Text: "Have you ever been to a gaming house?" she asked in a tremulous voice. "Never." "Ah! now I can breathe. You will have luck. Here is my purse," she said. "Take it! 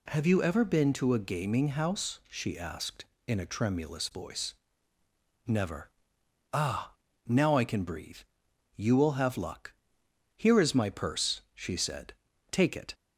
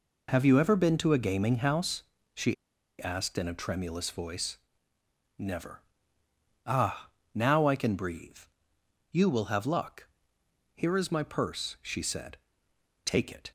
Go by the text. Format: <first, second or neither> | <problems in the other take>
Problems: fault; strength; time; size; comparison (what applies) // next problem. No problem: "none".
first | pauses between "she" and "asked"; noticeable; at 2.5 s; 0.48 s long